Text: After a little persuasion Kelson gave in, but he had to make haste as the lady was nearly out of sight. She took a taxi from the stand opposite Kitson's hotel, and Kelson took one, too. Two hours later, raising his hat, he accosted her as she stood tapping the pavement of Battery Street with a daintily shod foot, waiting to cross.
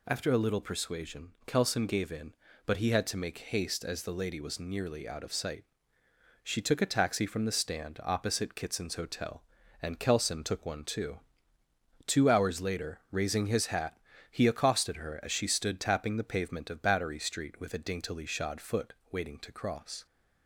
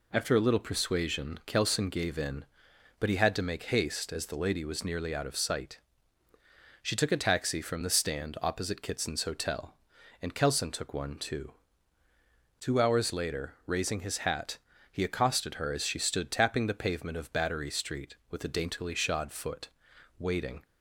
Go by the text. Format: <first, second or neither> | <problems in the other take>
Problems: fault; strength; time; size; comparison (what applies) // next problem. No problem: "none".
first | stops before "to cross"; at 20.6 s